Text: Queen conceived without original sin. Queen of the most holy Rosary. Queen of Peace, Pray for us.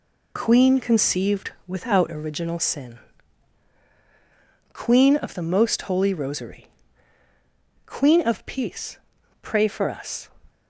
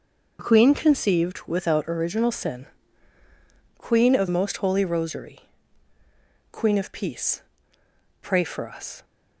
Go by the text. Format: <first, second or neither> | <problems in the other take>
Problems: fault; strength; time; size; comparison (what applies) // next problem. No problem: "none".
first | skips "the"; at 4.2 s